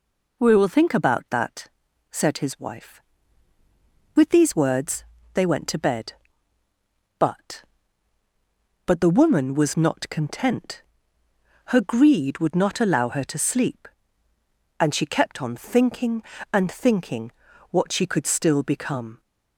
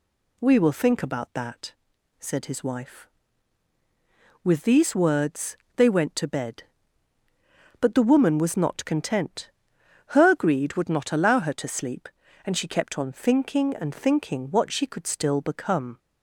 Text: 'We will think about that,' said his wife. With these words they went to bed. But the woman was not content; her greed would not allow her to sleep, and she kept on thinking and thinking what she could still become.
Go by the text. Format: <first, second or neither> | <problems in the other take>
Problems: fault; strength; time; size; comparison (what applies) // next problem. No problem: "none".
second | pauses between "words" and "they"; slight; at 5.0 s; 0.30 s long; slight in the second // says "But" twice; at 8.8 s // pauses between "thinking" and "what"; at 17.2 s; 0.40 s long